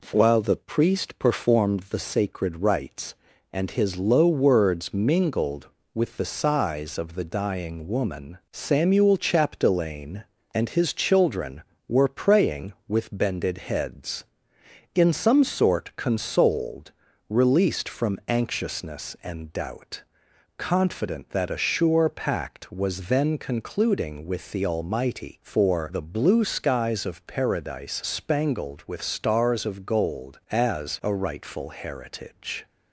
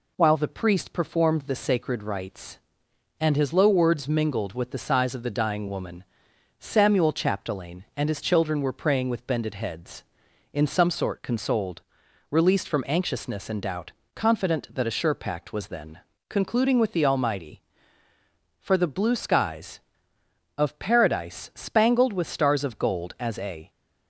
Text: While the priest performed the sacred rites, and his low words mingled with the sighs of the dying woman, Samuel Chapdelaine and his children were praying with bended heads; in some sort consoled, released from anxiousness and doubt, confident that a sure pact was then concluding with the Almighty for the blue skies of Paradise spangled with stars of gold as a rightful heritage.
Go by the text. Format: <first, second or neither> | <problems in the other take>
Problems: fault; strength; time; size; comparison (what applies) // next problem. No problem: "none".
first | pauses between "then" and "concluding"; slight; at 15.9 s; 0.30 s long // stops before "rightful heritage"; at 23.6 s